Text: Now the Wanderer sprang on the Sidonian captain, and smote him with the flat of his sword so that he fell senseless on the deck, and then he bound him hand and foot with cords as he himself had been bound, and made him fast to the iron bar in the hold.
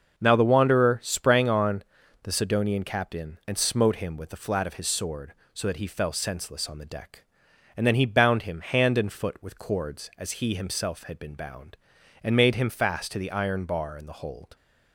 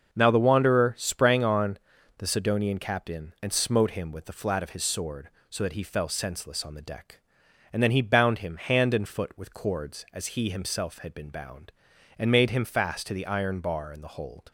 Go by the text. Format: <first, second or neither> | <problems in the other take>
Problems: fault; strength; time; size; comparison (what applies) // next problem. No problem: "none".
neither | starts louder than the rest; the same in both // pauses between "on" and "the"; the same in both